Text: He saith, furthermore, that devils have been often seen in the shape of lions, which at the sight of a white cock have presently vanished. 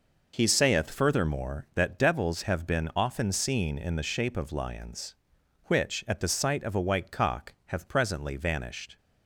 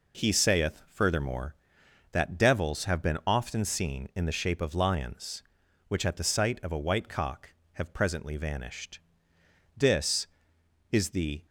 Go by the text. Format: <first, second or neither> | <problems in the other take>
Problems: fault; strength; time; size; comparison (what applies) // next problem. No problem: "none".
first | goes on to say "This is the"; strong; from 9.7 s on; 1.7 s long